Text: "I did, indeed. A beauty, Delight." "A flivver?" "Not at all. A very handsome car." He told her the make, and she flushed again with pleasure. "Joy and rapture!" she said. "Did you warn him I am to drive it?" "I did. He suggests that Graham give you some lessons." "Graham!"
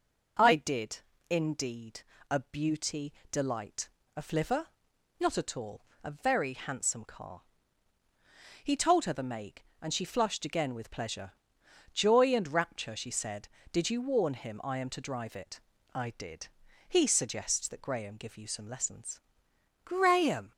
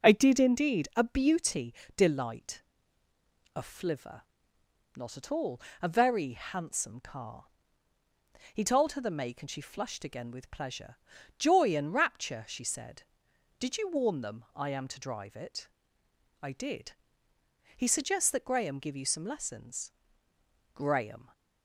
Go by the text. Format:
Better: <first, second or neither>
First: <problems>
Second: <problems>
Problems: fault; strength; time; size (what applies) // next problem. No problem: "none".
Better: first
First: none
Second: says "them" for "him"; at 14.1 s